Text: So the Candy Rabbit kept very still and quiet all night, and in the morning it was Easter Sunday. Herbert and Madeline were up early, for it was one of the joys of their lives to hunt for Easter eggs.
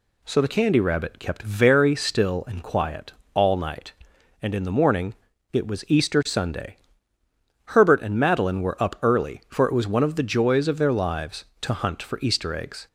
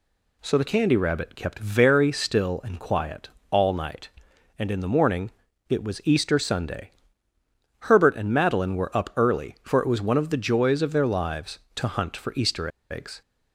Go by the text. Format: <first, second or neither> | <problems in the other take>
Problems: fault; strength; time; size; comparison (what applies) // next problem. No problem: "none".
first | pauses between "quiet" and "all"; slight; at 3.2 s; 0.22 s long; slight in the first // pauses between "morning" and "it"; at 5.3 s; 0.38 s long; also in the first // pauses between "Easter" and "eggs"; slight; at 12.6 s; 0.21 s long